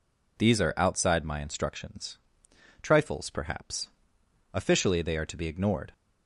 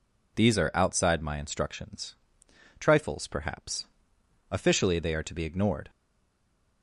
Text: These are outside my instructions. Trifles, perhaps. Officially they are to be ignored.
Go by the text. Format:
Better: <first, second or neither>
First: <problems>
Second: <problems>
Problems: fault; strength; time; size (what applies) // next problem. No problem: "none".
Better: first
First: none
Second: stays silent after the last word; slight; from 5.8 s on; 1.0 s long